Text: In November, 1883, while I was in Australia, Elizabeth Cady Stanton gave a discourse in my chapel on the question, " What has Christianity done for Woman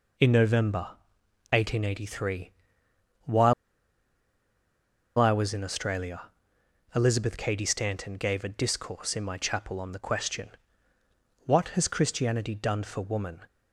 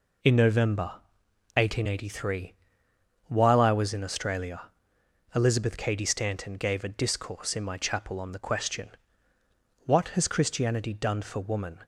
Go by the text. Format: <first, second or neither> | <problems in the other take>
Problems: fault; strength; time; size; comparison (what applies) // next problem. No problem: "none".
second | pauses between "while" and "I"; strong; at 3.5 s; 1.6 s long